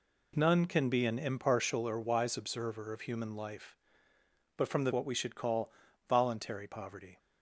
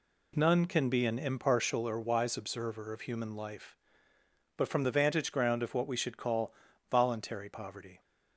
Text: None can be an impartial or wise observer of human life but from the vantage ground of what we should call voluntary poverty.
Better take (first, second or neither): second